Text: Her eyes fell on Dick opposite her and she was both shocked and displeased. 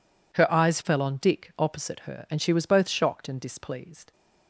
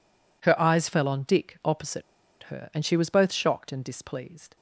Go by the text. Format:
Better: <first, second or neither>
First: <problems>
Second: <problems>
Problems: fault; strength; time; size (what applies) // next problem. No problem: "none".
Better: first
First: none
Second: pauses between "opposite" and "her"; at 2.0 s; 0.40 s long